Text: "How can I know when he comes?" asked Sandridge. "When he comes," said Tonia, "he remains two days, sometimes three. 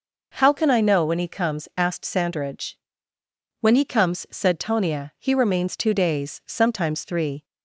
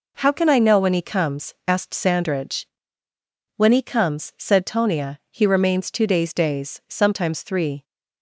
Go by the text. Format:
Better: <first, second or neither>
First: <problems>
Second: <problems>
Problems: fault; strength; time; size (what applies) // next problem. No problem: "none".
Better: first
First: none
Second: says "days" twice; at 6.3 s